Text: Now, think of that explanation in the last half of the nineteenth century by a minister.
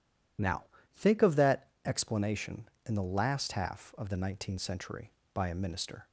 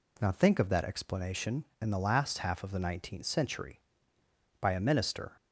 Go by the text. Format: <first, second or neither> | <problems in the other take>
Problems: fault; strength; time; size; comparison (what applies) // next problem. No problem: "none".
second | loses the start of "Now"; at 0.3 s; 25 ms // pauses between "that" and "explanation"; slight; at 1.6 s; 0.16 s long